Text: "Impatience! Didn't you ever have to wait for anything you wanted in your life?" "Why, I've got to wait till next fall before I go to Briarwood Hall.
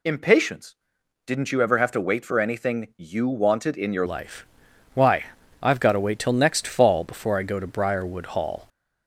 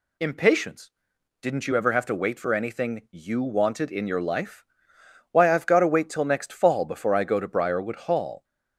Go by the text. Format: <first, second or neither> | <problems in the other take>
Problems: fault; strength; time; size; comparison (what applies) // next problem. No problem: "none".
second | changes voice at "life"; from 4.0 s on; 4.6 s long